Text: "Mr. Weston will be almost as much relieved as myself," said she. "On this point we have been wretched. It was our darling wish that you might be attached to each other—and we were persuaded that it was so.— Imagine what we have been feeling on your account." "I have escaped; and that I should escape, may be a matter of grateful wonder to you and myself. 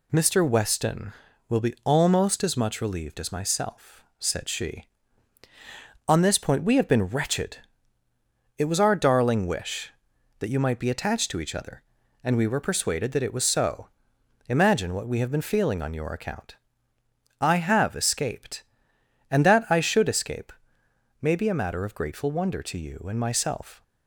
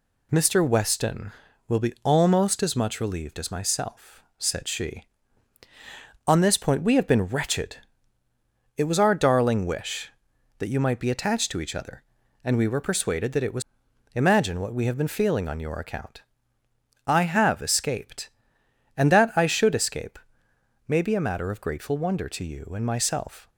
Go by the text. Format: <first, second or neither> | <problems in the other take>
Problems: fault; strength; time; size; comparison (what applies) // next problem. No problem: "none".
first | skips "so"; at 13.8 s